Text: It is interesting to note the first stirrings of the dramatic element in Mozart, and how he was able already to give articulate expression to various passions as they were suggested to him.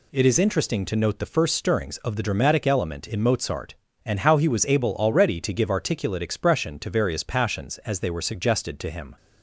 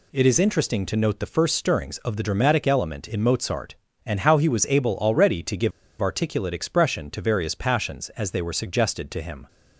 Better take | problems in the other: first | pauses between "give" and "articulate"; slight; at 5.7 s; 0.28 s long

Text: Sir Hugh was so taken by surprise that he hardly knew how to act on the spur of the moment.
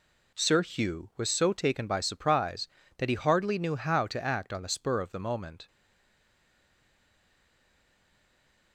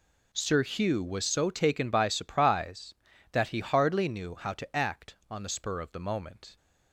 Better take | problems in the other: second | stays silent after the last word; strong; from 5.6 s on; 3.1 s long

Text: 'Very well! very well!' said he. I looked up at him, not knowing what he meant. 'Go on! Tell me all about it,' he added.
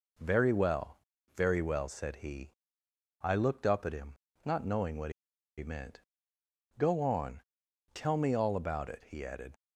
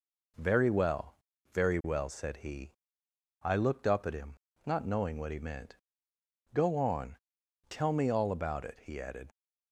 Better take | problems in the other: second | pauses between "what" and "he"; noticeable; at 5.1 s; 0.47 s long

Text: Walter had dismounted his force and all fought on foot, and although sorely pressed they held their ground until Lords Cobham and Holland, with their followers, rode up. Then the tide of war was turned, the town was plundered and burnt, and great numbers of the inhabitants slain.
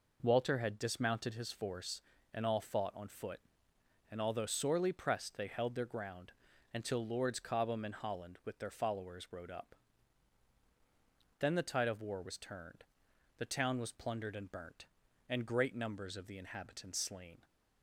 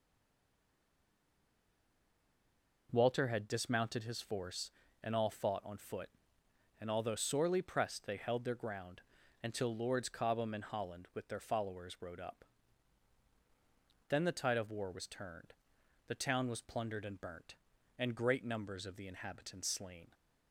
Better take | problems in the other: first | stays silent before the first word; strong; until 2.8 s; 2.8 s long // pauses between "ground" and "until"; at 9.0 s; 0.40 s long; also in the first

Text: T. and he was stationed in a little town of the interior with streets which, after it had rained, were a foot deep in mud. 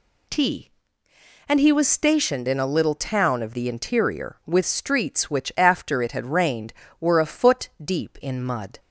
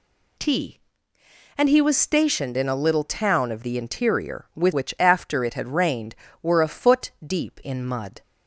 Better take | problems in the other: first | skips "streets"; at 4.7 s

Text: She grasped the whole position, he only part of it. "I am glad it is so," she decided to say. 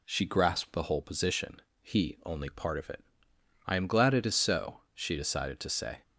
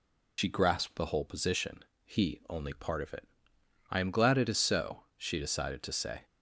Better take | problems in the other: first | loses the start of "She"; at 0.3 s; 105 ms

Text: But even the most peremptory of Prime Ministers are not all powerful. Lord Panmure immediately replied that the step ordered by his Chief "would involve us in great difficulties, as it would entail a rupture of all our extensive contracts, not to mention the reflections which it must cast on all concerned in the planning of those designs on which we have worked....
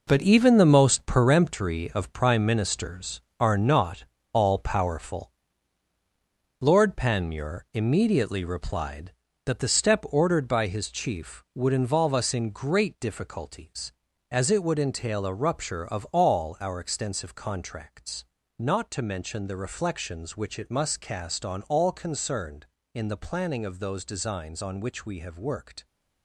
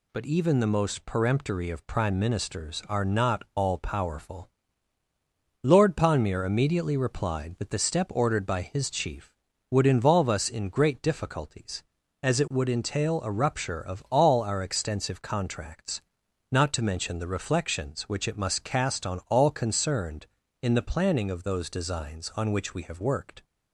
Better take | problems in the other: second | gets quieter; strong; throughout; 9 dB // pauses between "not" and "all"; slight; at 4.0 s; 0.28 s long

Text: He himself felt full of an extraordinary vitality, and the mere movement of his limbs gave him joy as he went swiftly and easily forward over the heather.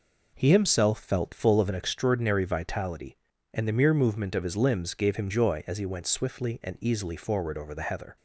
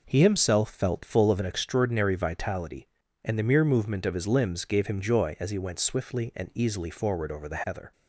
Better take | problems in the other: neither | none

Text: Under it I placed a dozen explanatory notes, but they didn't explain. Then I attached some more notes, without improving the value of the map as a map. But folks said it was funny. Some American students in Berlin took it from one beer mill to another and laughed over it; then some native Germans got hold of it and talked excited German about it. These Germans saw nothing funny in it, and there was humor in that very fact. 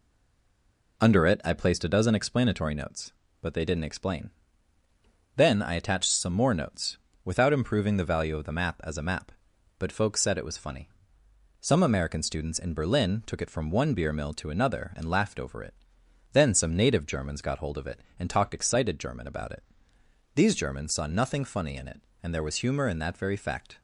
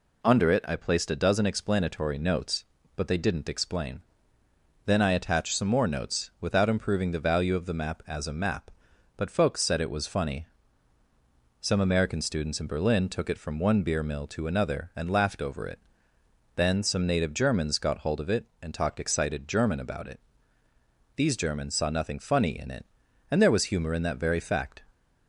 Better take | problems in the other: second | stays silent before the first word; until 0.9 s; 0.9 s long

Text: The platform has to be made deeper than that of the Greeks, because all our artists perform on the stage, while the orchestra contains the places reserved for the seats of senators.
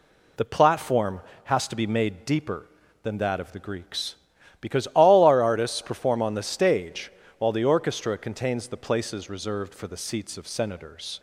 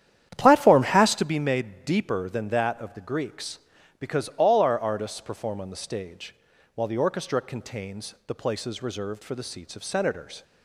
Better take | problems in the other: first | starts louder than the rest; strong; until 1.3 s; 10 dB

